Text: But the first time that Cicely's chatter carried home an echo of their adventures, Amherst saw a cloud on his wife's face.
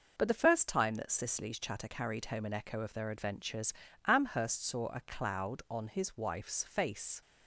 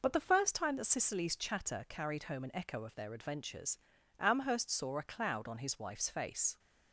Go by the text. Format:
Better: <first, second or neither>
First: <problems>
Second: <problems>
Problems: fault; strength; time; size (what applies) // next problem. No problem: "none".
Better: neither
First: none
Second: none